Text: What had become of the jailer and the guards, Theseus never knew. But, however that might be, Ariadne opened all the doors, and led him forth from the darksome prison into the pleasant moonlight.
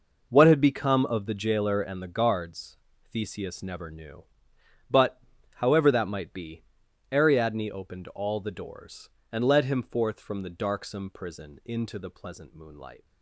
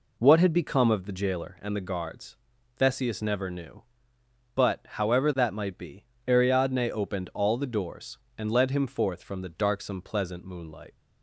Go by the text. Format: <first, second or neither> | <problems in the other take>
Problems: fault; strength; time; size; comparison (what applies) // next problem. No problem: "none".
first | skips "prison into the"; at 10.0 s